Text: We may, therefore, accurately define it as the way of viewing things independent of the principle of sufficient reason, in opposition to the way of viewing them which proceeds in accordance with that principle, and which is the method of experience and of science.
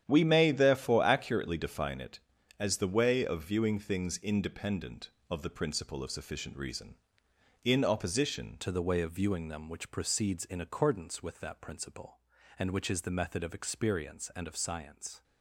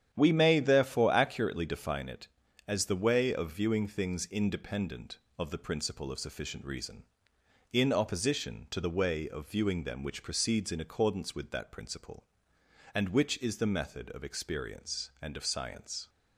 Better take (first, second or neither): second